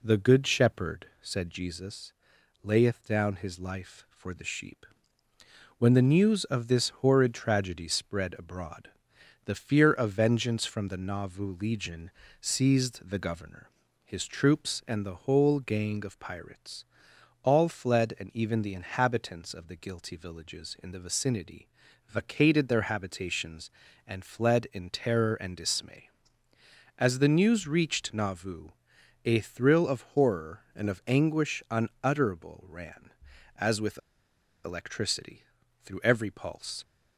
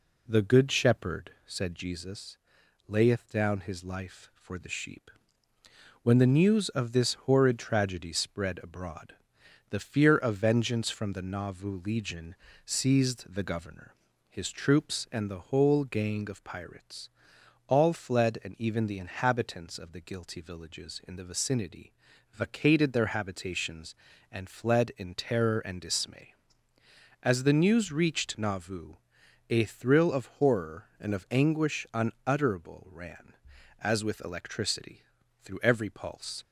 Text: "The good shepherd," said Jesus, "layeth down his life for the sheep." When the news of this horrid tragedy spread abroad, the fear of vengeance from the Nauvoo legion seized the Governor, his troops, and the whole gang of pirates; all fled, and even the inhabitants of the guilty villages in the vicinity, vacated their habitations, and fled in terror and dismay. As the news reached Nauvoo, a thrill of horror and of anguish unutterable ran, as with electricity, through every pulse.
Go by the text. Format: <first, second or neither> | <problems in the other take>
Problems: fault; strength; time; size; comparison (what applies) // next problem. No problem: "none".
second | pauses between "legion" and "seized"; slight; at 12.1 s; 0.30 s long; slight in the second // pauses between "with" and "electricity"; noticeable; at 33.9 s; 0.64 s long